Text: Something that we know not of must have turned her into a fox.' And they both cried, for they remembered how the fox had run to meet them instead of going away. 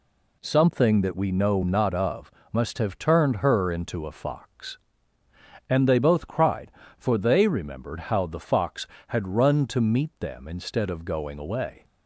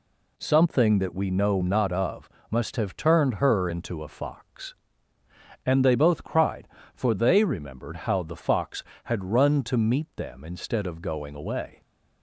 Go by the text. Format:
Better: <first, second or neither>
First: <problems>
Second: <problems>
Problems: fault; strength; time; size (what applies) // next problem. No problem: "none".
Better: neither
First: pauses between "of" and "must"; slight; at 2.3 s; 0.22 s long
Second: pauses between "of" and "must"; slight; at 2.2 s; 0.22 s long